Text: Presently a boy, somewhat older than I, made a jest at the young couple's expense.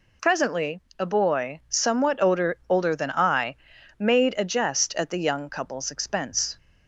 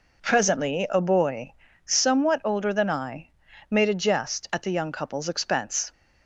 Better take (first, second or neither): second